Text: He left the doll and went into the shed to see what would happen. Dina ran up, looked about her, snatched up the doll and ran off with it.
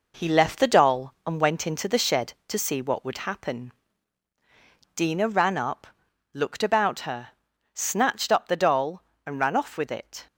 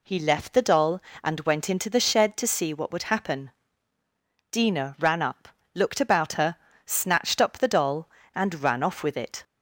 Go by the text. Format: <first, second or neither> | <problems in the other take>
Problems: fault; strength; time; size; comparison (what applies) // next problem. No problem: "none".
second | gets quieter; noticeable; throughout; 5 dB